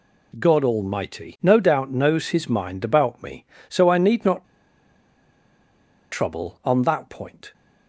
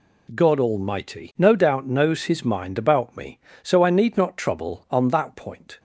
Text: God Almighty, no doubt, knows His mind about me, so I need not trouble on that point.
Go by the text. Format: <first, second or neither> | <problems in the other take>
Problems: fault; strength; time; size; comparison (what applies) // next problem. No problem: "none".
second | pauses between "not" and "trouble"; strong; at 4.4 s; 1.6 s long